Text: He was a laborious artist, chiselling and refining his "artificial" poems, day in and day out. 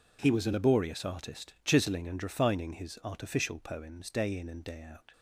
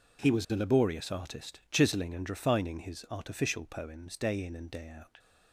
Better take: neither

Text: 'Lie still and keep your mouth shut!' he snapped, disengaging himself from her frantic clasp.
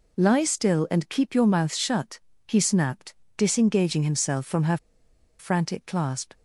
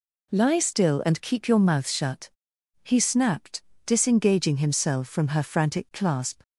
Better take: second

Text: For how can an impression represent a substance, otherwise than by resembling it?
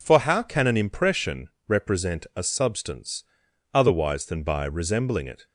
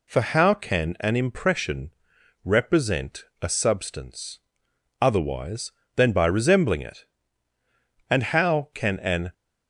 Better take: first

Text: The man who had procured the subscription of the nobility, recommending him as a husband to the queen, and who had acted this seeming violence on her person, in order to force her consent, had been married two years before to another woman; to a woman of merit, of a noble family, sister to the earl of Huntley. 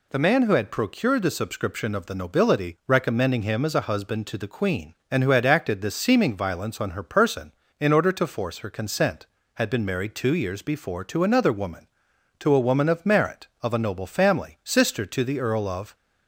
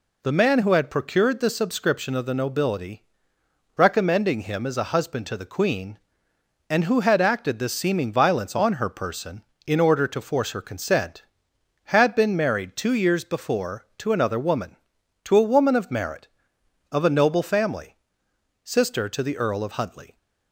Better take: second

